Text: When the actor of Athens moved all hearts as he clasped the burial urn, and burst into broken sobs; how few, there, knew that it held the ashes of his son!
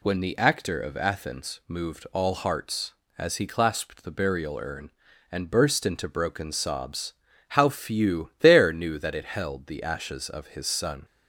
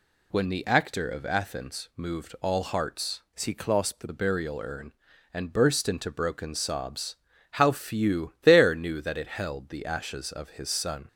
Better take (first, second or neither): first